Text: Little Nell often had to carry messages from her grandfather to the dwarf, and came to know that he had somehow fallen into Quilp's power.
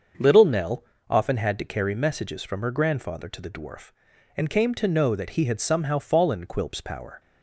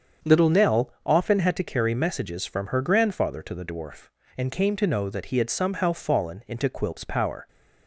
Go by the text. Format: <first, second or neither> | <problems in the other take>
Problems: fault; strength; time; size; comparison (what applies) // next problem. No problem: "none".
second | starts louder than the rest; until 1.4 s; 6.5 dB; strong in the second // pauses between "Nell" and "often"; slight; at 0.8 s; 0.28 s long // skips "into"; at 6.4 s